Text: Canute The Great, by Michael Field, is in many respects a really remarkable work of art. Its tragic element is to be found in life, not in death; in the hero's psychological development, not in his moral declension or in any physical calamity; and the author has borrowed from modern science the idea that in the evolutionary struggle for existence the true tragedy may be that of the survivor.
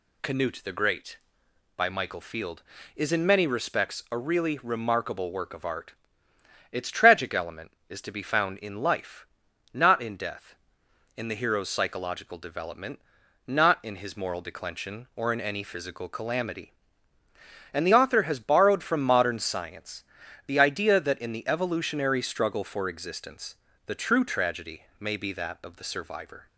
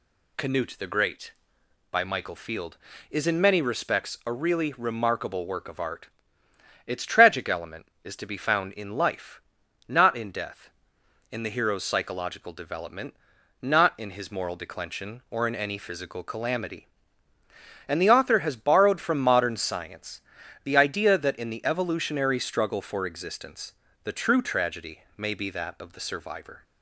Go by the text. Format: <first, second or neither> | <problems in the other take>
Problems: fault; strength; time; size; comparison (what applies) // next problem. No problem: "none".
neither | pauses between "science" and "the"; the same in both // pauses between "existence" and "the"; slight; the same in both // pauses between "tragedy" and "may"; slight; the same in both